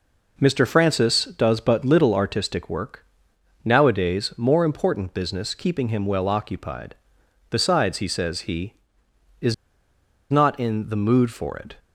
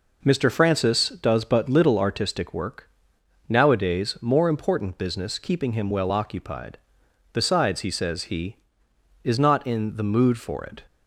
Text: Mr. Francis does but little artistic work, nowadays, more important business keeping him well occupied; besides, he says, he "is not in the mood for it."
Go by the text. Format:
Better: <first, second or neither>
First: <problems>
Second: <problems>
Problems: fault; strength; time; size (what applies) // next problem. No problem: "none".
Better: second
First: pauses between "is" and "not"; noticeable; at 9.5 s; 0.76 s long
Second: none